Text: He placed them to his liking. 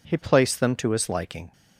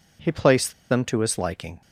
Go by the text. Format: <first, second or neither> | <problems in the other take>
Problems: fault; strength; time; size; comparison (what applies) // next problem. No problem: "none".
first | pauses between "placed" and "them"; slight; at 0.7 s; 0.17 s long